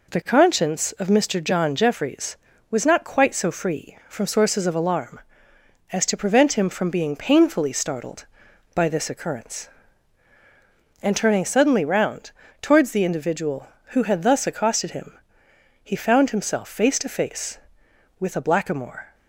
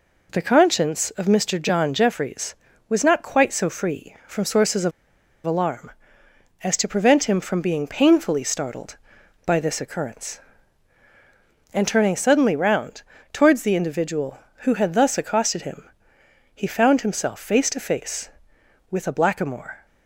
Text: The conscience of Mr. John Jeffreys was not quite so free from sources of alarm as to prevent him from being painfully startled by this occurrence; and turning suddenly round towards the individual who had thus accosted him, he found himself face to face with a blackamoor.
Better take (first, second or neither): first